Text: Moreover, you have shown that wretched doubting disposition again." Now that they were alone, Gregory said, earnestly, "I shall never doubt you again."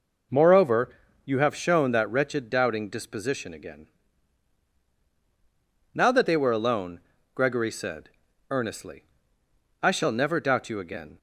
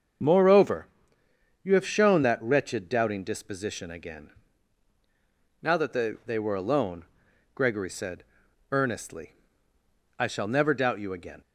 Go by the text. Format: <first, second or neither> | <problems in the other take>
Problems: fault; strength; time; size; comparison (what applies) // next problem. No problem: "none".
first | starts louder than the rest; until 2.0 s; 6.5 dB // says "they" twice; at 6.2 s